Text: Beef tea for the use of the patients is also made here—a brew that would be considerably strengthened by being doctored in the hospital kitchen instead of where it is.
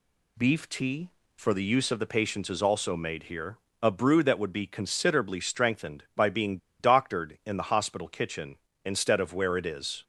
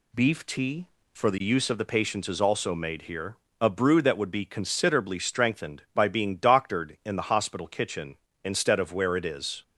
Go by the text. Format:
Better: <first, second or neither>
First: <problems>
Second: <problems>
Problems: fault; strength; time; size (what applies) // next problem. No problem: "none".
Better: second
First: pauses between "being" and "doctored"; slight; at 6.5 s; 0.21 s long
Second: none